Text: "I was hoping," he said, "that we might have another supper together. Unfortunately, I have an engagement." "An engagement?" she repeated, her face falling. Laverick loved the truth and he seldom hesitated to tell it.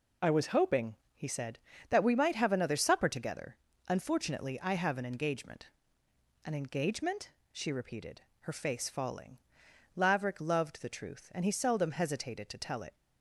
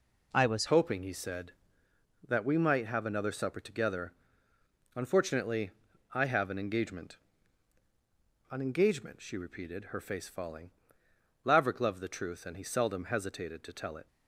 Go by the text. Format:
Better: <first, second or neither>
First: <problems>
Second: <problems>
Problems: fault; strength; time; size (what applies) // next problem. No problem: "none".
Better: first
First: none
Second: changes voice at "hoping"; from 0.6 s on; 13.4 s long